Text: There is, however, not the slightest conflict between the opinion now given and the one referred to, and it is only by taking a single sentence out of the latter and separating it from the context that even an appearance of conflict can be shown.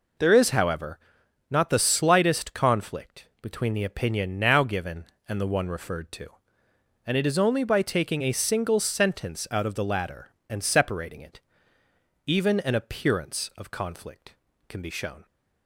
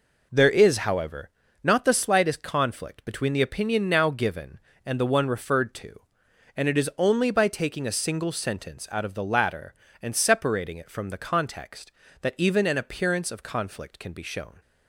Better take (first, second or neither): second